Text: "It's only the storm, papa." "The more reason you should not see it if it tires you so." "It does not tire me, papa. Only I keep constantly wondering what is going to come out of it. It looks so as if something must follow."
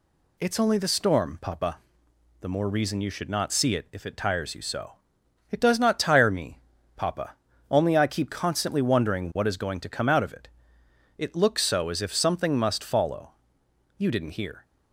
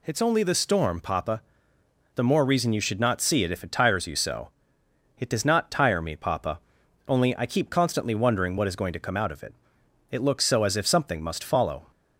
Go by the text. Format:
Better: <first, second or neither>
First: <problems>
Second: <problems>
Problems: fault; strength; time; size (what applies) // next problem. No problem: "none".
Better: second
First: goes on to say "You didn't hear"; noticeable; from 13.9 s on; 0.66 s long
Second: none